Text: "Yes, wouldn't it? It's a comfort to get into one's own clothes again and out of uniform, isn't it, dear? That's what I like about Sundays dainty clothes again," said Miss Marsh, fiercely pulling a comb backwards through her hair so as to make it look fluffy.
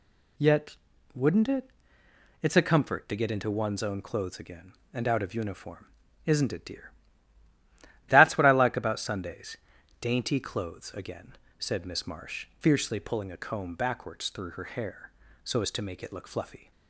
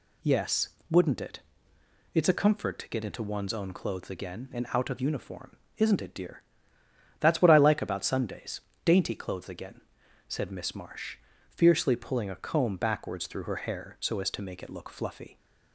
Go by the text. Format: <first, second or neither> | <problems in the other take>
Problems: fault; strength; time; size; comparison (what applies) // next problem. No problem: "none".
second | says "Yet" for "Yes"; at 0.3 s // pauses between "Sundays" and "dainty"; at 9.5 s; 0.44 s long; slight in the second